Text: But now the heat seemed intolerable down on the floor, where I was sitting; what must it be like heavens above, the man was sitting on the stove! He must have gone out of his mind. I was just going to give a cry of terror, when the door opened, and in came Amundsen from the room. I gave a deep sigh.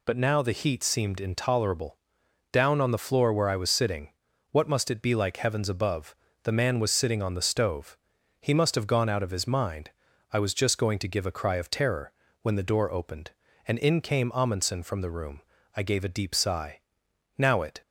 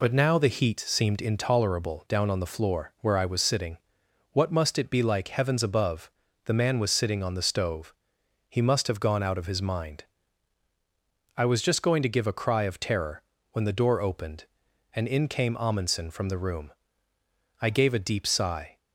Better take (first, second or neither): second